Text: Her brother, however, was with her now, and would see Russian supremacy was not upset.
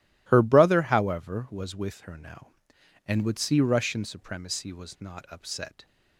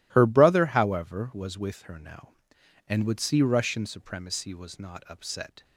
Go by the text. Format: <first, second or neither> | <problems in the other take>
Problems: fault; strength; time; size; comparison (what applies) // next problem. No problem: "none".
neither | none